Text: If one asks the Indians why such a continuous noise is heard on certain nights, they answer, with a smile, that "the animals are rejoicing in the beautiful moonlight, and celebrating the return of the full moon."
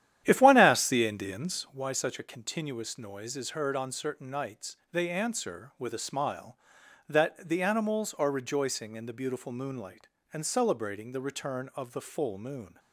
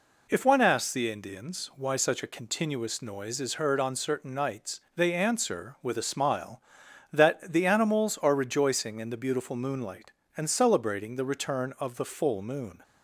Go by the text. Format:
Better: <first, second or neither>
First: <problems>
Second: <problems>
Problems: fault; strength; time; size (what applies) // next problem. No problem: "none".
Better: second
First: starts louder than the rest; strong; until 1.8 s; 11 dB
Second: none